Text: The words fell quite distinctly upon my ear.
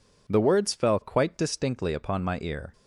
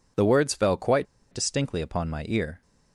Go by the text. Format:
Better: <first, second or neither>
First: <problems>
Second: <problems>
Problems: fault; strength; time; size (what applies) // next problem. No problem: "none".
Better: first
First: none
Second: pauses between "quite" and "distinctly"; slight; at 1.0 s; 0.27 s long